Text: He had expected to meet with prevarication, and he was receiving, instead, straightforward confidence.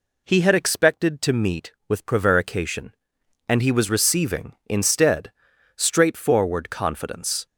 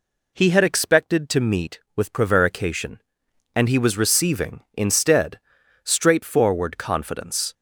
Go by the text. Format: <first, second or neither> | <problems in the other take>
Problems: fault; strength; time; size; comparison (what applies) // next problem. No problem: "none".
neither | none